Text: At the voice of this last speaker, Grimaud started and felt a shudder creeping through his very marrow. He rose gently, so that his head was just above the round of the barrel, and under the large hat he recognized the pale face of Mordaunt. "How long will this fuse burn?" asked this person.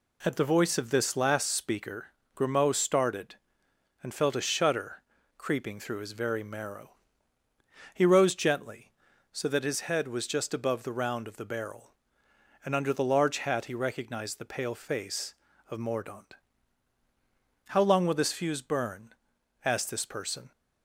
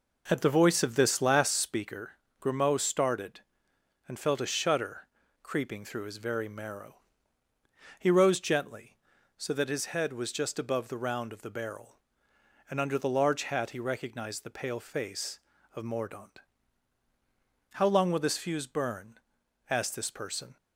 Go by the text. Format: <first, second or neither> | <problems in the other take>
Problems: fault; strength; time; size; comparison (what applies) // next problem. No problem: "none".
first | starts louder than the rest; noticeable; until 1.7 s; 5 dB // pauses between "shudder" and "creeping"; at 5.0 s; 0.38 s long; also in the first